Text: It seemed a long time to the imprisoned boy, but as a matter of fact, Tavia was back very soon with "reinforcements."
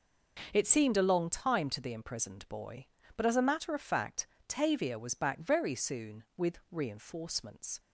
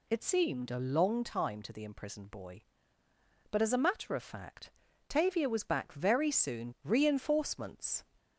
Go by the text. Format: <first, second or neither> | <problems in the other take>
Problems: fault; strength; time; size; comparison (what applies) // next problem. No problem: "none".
first | skips "with"; at 6.7 s